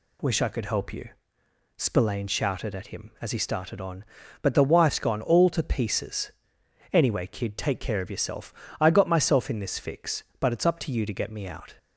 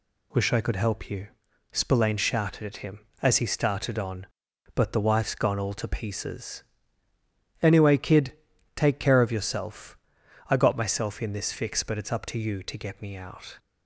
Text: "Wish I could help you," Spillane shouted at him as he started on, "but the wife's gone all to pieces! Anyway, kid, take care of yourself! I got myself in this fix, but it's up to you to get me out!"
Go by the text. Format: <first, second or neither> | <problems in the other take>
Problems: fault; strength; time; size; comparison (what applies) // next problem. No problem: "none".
neither | none